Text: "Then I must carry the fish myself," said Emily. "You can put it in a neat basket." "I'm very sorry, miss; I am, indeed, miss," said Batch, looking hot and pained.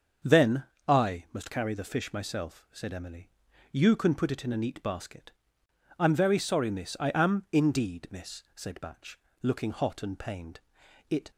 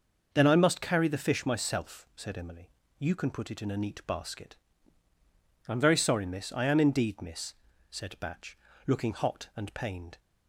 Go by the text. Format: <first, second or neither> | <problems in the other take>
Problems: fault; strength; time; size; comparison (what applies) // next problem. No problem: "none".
second | starts louder than the rest; until 1.5 s; 7 dB; noticeable in the second // pauses between "Then" and "I"; slight; at 0.6 s; 0.24 s long // goes on to say "It"; slight; from 11.0 s on; 0.22 s long